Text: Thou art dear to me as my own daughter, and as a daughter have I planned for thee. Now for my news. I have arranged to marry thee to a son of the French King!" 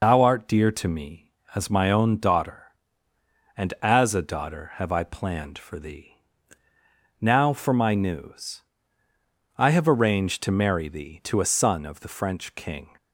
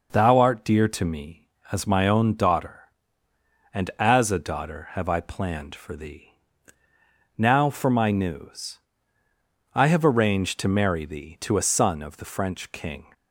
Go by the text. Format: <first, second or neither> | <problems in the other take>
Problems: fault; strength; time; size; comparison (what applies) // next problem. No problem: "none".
second | loses the start of "Thou"; at 0.0 s; 90 ms